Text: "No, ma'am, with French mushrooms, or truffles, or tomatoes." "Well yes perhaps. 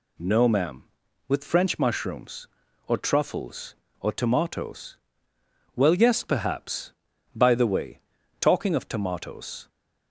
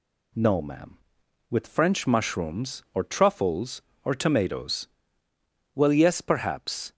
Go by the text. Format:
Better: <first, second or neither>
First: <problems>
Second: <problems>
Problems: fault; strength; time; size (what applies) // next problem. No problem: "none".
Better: second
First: goes on to say "By the way talking of tomatoes"; strong; from 7.3 s on; 2.3 s long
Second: none